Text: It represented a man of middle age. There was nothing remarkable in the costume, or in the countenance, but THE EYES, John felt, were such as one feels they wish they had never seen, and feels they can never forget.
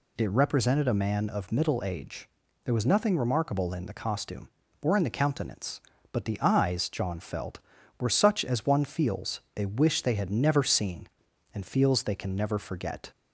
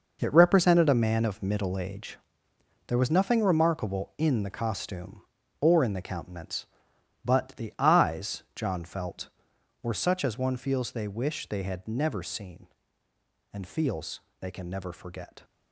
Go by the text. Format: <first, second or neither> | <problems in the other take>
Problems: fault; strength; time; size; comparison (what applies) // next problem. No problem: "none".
first | gets quieter; strong; throughout; 10.5 dB // pauses between "feels" and "they"; slight; at 14.2 s; 0.20 s long